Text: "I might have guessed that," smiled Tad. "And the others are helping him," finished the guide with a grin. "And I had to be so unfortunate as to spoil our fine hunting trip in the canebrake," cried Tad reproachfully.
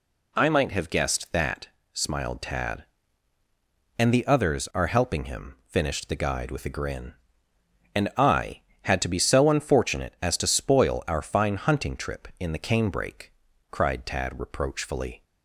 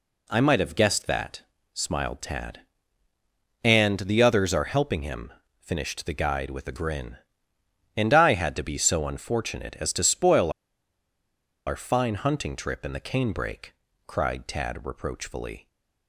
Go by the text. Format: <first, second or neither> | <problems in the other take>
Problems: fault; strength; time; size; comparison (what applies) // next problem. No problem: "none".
first | pauses between "spoil" and "our"; at 10.5 s; 1.1 s long